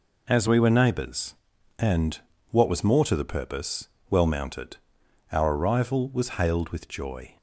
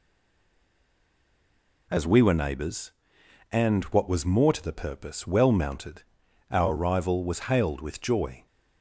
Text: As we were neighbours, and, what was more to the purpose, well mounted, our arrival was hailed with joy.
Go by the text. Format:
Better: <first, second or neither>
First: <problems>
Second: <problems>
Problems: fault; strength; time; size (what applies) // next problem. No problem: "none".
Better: first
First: none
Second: stays silent before the first word; noticeable; until 1.8 s; 1.8 s long